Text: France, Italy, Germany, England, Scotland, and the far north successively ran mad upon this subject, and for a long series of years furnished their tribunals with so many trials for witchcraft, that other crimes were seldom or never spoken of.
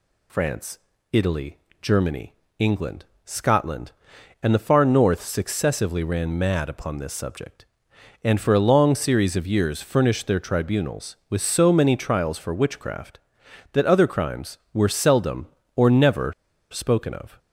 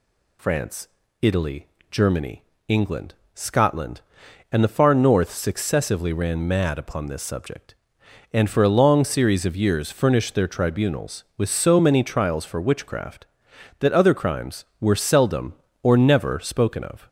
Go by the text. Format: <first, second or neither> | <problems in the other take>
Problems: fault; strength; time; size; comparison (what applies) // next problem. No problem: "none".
second | pauses between "never" and "spoken"; at 16.3 s; 0.39 s long